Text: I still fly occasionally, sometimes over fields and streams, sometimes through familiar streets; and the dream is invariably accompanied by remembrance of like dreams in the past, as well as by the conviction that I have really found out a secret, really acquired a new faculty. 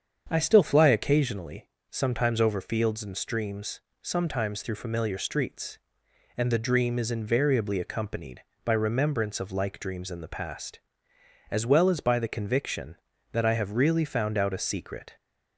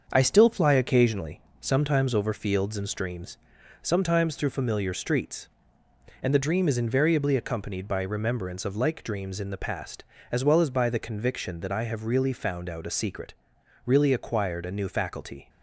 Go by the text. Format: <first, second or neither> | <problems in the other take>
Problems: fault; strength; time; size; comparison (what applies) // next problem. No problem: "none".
second | starts louder than the rest; strong; until 1.3 s; 7.5 dB; also in the second // stops before "really acquired a new faculty"; at 15.1 s